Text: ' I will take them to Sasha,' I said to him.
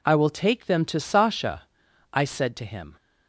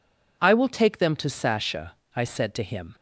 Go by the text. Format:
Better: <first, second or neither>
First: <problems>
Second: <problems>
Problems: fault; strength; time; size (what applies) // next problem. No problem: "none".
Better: neither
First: none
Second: none